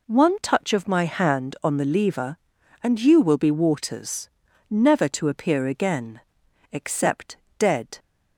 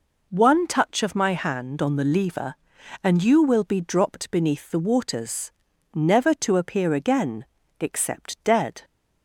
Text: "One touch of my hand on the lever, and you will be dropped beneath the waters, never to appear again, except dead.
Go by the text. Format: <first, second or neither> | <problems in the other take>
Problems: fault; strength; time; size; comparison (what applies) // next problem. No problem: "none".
second | skips "dropped beneath the"; at 3.4 s // pauses between "except" and "dead"; slight; at 7.3 s; 0.22 s long